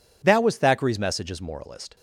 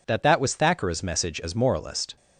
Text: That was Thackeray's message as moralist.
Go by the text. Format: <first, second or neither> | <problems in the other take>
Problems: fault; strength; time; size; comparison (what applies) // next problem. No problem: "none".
first | says "That" twice; at 0.2 s